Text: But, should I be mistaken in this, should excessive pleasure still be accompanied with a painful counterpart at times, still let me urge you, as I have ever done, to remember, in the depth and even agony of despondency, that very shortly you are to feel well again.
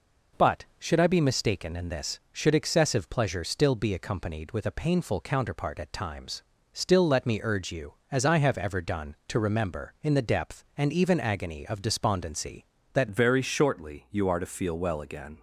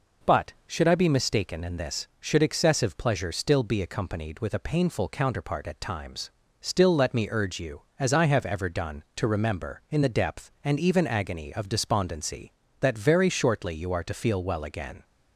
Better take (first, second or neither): second